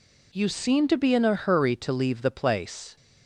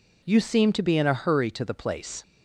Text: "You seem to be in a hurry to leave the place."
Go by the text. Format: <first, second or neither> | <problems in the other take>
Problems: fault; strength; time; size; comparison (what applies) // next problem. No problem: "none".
first | skips "leave"; at 1.6 s